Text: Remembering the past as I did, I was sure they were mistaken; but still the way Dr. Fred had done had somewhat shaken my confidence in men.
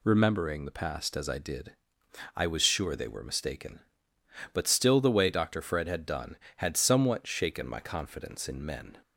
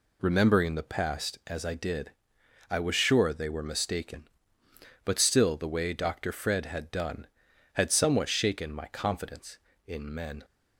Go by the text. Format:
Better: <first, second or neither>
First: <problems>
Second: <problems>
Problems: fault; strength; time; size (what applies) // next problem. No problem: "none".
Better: neither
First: none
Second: none